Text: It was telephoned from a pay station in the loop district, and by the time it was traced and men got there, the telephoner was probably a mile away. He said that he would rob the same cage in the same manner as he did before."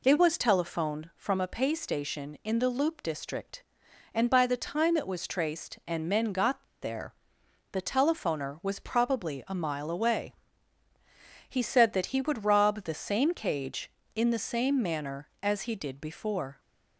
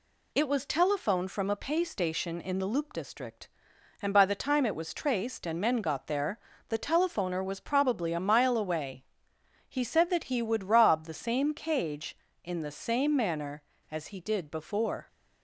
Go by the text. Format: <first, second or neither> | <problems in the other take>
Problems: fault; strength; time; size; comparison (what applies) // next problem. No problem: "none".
second | pauses between "got" and "there"; slight; at 6.6 s; 0.17 s long